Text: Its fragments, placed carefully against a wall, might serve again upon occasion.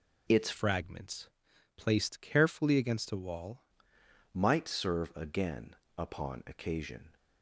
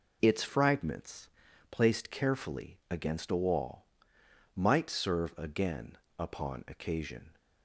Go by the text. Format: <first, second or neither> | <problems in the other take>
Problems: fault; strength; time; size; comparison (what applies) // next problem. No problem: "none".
second | changes voice from "fragments" to "wall"; from 0.5 to 3.6 s; 3.1 s long // pauses between "again" and "upon"; slight; at 5.7 s; 0.22 s long; slight in the second